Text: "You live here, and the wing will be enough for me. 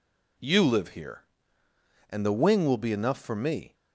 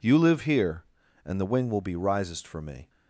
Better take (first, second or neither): first